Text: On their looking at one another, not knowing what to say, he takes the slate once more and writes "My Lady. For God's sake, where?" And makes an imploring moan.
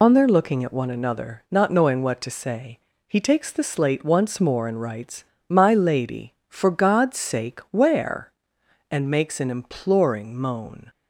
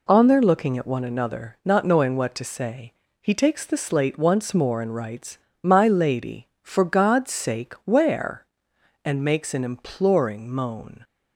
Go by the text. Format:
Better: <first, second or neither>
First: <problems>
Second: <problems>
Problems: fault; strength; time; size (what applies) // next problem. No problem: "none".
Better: second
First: loses the start of "On"; at 0.0 s; 70 ms // pauses between "writes" and "My"; slight; at 5.2 s; 0.24 s long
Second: pauses between "writes" and "My"; slight; at 5.3 s; 0.24 s long